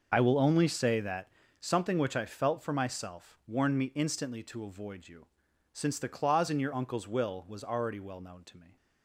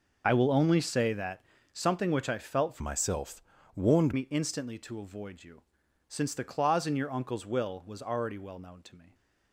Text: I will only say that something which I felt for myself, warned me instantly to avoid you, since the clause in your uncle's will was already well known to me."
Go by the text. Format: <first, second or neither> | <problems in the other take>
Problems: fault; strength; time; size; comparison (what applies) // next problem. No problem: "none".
first | pauses between "that" and "something"; slight; at 1.4 s; 0.28 s long; slight in the first // changes voice from "myself" to "warned"; from 2.8 to 4.1 s; 1.3 s long